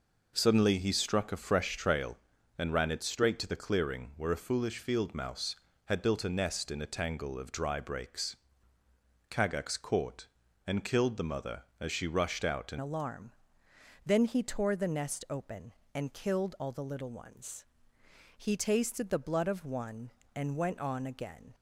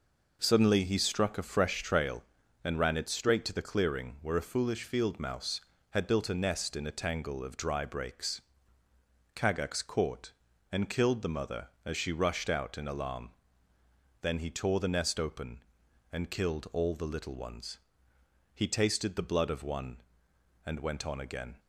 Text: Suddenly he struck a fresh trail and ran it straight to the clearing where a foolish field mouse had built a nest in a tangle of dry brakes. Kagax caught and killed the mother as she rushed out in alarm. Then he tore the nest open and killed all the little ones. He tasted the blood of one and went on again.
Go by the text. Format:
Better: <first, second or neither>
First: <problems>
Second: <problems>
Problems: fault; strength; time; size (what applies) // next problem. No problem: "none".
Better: second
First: changes voice at "alarm"; from 12.7 s on; 8.8 s long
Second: none